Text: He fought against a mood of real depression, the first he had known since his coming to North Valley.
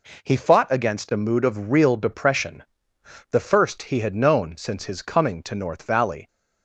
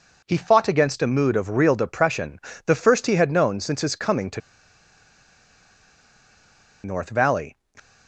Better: first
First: none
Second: pauses between "to" and "North"; strong; at 4.4 s; 2.4 s long

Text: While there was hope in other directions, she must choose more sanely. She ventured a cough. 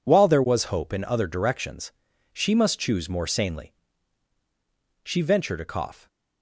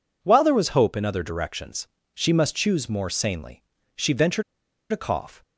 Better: first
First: none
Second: pauses between "ventured" and "a"; noticeable; at 4.4 s; 0.50 s long

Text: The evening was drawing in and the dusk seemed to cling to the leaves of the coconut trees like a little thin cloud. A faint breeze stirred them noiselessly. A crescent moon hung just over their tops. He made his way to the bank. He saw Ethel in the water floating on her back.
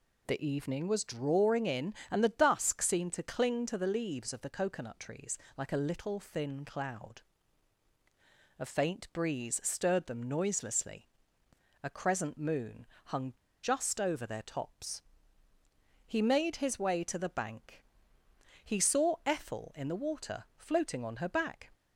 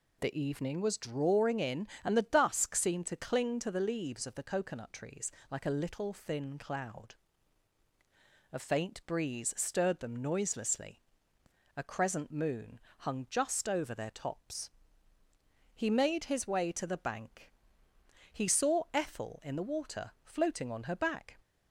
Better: second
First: pauses between "trees" and "like"; slight; at 5.3 s; 0.20 s long // pauses between "moon" and "hung"; slight; at 12.8 s; 0.18 s long // pauses between "hung" and "just"; slight; at 13.3 s; 0.30 s long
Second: pauses between "trees" and "like"; slight; at 5.3 s; 0.20 s long // pauses between "moon" and "hung"; slight; at 12.8 s; 0.18 s long

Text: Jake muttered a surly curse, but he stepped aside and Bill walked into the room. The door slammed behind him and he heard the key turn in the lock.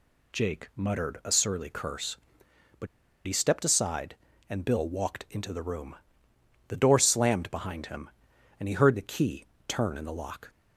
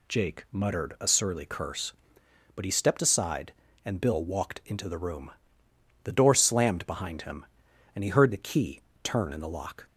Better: second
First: pauses between "but" and "he"; at 2.8 s; 0.39 s long // pauses between "key" and "turn"; slight; at 9.4 s; 0.22 s long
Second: pauses between "key" and "turn"; slight; at 8.8 s; 0.22 s long

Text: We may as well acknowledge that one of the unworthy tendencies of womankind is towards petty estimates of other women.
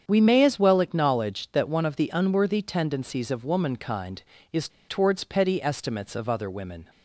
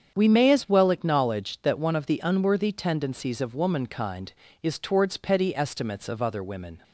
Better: second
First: starts louder than the rest; strong; until 1.1 s; 8 dB // pauses between "is" and "towards"; slight; at 4.6 s; 0.20 s long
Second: starts louder than the rest; strong; until 1.2 s; 8 dB

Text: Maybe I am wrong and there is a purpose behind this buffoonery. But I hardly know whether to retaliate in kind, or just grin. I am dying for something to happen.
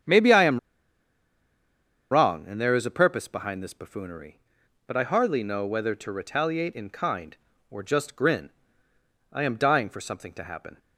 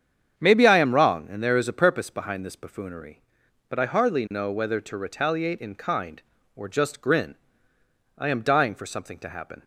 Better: second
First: starts louder than the rest; strong; until 2.5 s; 8 dB // pauses between "am" and "wrong"; strong; at 0.5 s; 1.5 s long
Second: starts louder than the rest; strong; until 1.4 s; 8 dB

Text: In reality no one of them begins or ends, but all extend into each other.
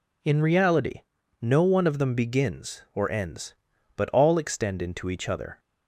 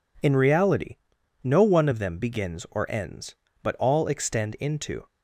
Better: first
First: pauses between "reality" and "no"; at 1.0 s; 0.40 s long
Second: pauses between "reality" and "no"; noticeable; at 0.9 s; 0.48 s long // stops before "each other"; at 5.0 s

